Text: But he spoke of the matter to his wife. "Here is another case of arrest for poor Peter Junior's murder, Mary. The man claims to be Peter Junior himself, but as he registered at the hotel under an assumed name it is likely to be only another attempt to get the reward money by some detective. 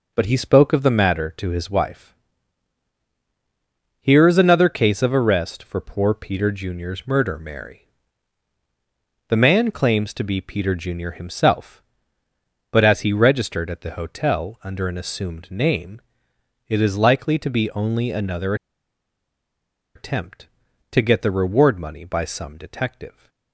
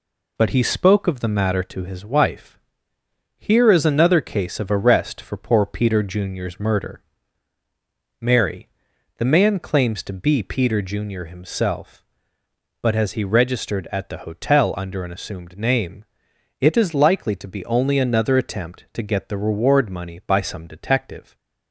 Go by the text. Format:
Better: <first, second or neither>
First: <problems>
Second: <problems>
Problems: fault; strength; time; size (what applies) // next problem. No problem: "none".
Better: second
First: pauses between "name" and "it"; noticeable; at 16.0 s; 0.66 s long // pauses between "another" and "attempt"; strong; at 18.5 s; 1.4 s long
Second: pauses between "name" and "it"; noticeable; at 16.0 s; 0.56 s long